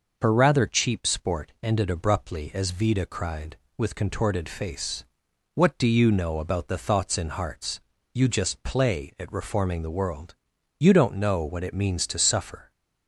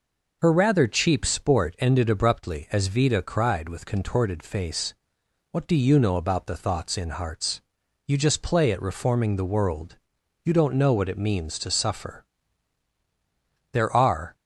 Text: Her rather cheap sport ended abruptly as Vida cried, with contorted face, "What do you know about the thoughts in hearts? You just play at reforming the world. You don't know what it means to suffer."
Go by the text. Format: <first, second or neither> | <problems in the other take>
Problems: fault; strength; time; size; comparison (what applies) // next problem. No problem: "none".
first | goes on to say "There are"; noticeable; from 13.7 s on; 0.64 s long